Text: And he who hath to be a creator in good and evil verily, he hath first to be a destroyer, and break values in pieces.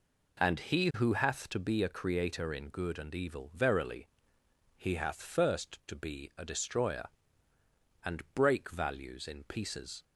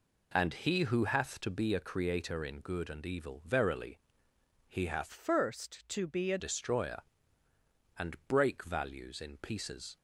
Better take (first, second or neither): first